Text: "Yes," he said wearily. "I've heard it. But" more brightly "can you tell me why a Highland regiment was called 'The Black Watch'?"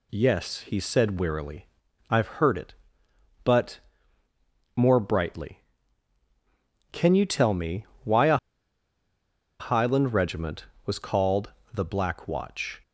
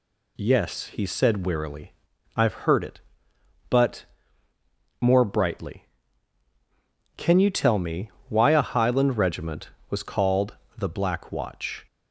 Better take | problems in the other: second | pauses between "But" and "more"; noticeable; at 3.7 s; 0.96 s long; noticeable in the second // pauses between "me" and "why"; slight; at 7.8 s; 0.20 s long; slight in the second // pauses between "a" and "Highland"; at 8.3 s; 1.2 s long // pauses between "called" and "The"; slight; at 11.5 s; 0.20 s long; slight in the second

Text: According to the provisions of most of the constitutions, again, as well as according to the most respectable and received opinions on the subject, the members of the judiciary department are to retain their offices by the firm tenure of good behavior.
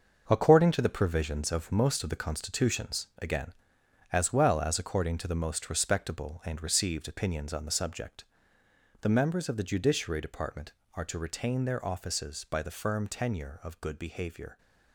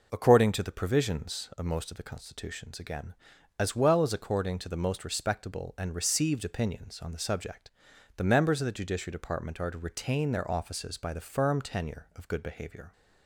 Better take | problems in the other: second | gets quieter; strong; throughout; 8.5 dB

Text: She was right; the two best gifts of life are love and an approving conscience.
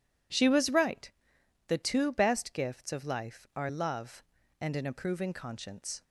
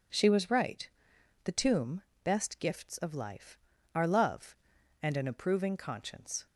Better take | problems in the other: first | says "tomb" for "two"; at 1.5 s

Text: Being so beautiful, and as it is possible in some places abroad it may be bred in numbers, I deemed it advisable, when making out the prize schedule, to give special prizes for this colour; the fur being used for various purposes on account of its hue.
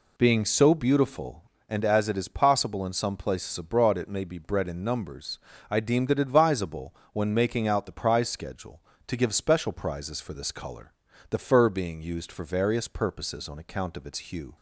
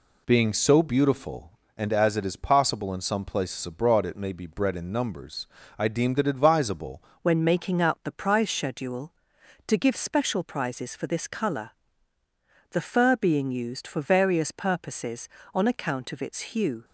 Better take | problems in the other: first | changes voice at "when"; from 7.2 s on; 9.6 s long

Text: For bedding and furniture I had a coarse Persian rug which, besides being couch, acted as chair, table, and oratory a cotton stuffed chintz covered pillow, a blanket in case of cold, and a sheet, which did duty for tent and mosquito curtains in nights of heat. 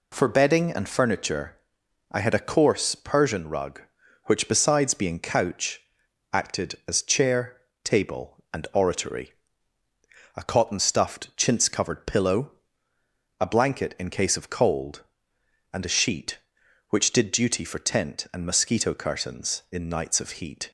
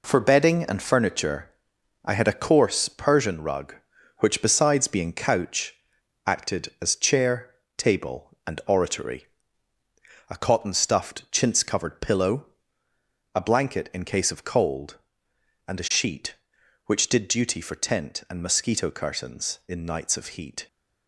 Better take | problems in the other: first | gets quieter; strong; throughout; 7 dB // pauses between "furniture" and "I"; noticeable; at 1.4 s; 0.56 s long; noticeable in the first // pauses between "oratory" and "a"; at 9.2 s; 1.0 s long; also in the first

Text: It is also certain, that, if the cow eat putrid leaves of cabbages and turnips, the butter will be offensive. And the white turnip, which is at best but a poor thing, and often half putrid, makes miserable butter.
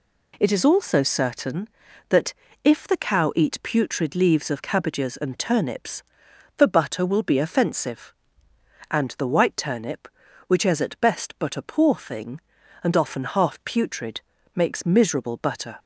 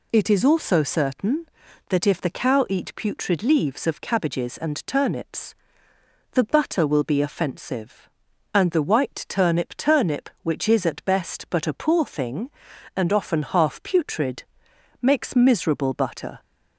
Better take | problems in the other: first | says "turnip" twice; at 9.7 s

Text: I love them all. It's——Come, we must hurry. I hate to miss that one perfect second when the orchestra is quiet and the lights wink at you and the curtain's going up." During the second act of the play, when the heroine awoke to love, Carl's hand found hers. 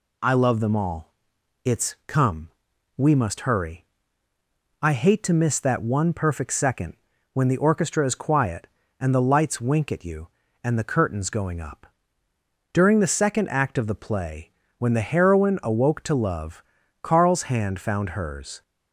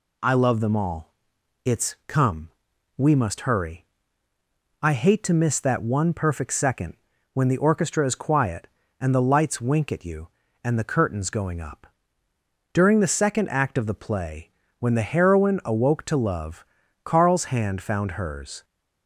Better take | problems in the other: neither | pauses between "second" and "when"; the same in both

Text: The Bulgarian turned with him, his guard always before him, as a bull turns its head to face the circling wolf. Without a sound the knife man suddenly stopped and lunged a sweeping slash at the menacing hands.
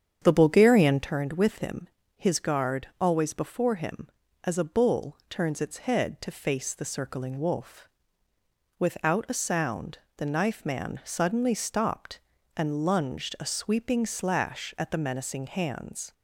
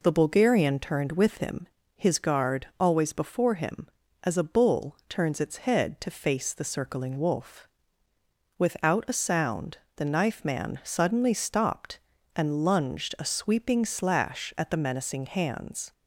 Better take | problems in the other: second | starts louder than the rest; strong; until 1.1 s; 8 dB // pauses between "sound" and "the"; slight; at 9.9 s; 0.18 s long; slight in the second

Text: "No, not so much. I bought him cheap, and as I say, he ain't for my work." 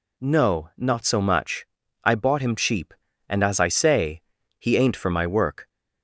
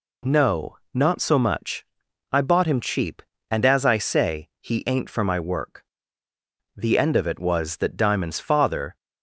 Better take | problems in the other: first | goes on to say "The end of it was that Diamond's father"; strong; from 6.7 s on; 2.2 s long

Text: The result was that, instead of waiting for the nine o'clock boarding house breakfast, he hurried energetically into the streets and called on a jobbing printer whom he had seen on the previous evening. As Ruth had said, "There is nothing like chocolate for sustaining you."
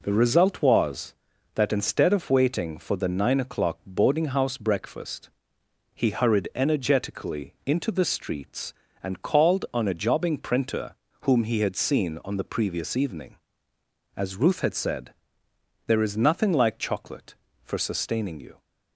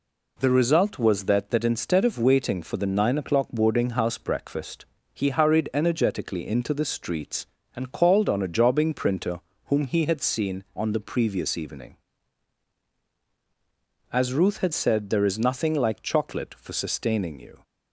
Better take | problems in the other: first | says "that" twice; at 1.4 s // pauses between "printer" and "whom"; slight; at 9.3 s; 0.26 s long; slight in the first

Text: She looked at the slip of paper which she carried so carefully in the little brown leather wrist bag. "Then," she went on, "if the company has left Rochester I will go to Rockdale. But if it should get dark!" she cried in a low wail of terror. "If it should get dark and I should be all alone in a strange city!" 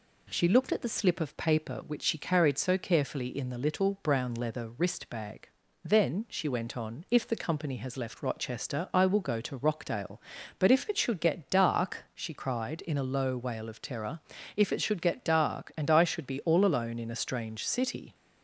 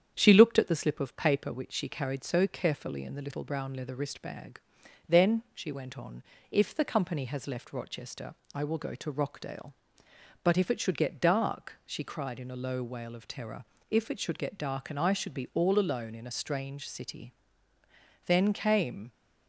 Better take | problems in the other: first | starts louder than the rest; strong; until 1.1 s; 8.5 dB // pauses between "Rochester" and "I"; slight; at 8.3 s; 0.20 s long // goes on to say "Then came"; noticeable; from 18.2 s on; 0.86 s long

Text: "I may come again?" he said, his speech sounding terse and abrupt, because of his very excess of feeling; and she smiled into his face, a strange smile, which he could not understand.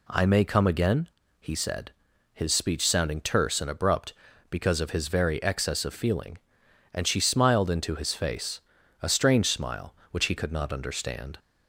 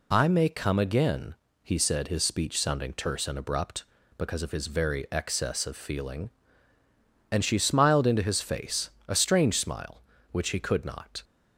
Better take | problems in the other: first | stops before "understand"; at 11.2 s

